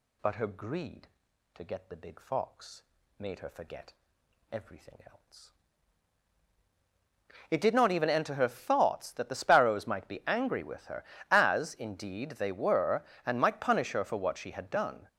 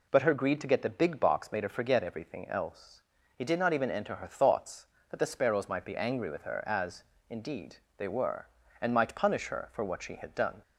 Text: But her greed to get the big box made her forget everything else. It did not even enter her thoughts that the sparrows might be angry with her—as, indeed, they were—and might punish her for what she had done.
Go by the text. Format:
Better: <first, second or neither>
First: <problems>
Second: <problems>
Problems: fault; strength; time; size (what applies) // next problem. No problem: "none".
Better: second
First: says "fox" for "box"; at 2.1 s // pauses between "forget" and "everything"; noticeable; at 3.9 s; 0.58 s long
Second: none